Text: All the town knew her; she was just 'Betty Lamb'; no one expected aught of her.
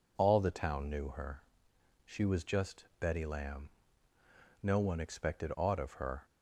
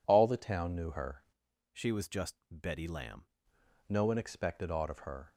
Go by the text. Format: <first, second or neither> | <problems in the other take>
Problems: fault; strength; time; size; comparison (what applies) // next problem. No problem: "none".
first | changes voice from "she" to "Lamb"; from 1.7 to 3.2 s; 1.5 s long